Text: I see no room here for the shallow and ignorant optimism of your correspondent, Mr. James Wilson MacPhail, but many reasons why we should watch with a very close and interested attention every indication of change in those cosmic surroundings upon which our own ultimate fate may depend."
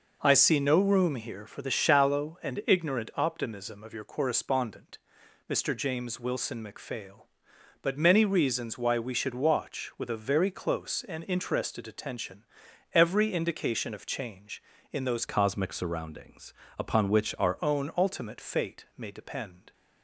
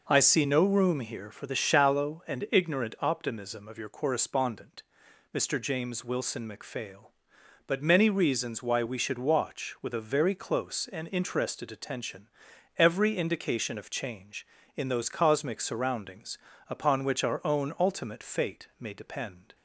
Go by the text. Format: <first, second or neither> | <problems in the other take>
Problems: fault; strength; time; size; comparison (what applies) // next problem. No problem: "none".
second | pauses between "attention" and "every"; noticeable; at 12.4 s; 0.48 s long; noticeable in the second // changes voice from "cosmic" to "our"; from 15.2 to 17.5 s; 2.3 s long // pauses between "surroundings" and "upon"; slight; at 16.5 s; 0.24 s long; slight in the second